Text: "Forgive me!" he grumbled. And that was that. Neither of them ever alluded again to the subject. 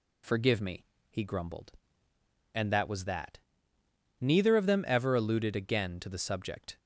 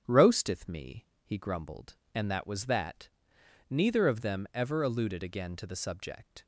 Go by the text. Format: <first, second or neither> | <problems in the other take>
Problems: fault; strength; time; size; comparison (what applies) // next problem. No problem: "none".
first | starts louder than the rest; strong; until 1.0 s; 8.5 dB // says "Roasteth" for "Forgive"; at 0.0 s